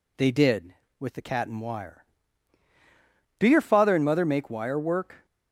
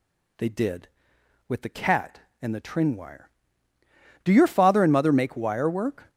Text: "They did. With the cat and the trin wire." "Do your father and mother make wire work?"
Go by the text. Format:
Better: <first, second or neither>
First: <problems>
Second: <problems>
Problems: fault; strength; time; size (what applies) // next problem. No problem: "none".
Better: second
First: skips "the trin"; at 1.5 s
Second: none